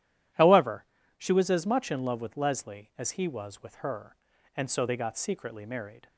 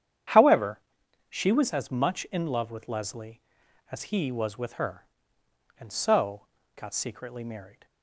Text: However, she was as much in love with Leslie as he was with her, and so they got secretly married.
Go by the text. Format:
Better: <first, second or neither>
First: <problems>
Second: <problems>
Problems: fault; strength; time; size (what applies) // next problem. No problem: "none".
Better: first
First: none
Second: starts louder than the rest; strong; until 1.8 s; 9 dB // skips "they"; at 6.5 s